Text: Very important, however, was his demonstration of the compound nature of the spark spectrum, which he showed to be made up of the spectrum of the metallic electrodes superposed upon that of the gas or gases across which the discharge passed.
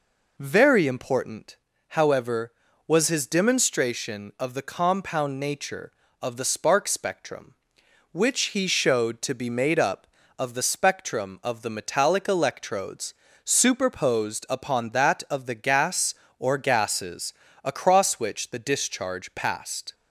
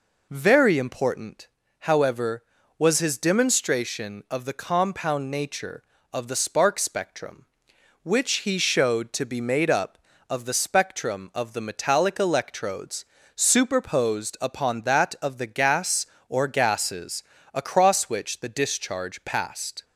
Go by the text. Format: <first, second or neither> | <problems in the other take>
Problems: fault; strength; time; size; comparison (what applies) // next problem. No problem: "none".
neither | pauses between "electrodes" and "superposed"; slight; the same in both // pauses between "gases" and "across"; slight; the same in both